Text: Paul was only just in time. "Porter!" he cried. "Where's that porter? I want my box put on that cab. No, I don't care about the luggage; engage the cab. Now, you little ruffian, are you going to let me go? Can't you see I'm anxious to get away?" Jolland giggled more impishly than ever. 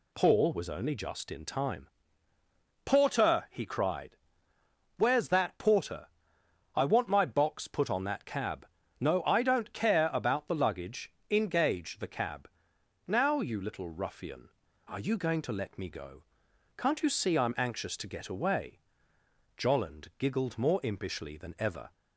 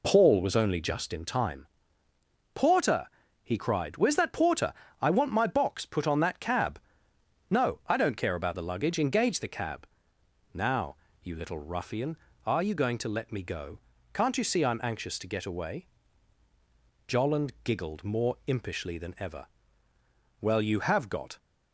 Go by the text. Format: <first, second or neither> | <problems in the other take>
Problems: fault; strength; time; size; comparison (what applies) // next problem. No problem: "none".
first | goes on to say "Well you have got"; noticeable; from 20.3 s on; 0.98 s long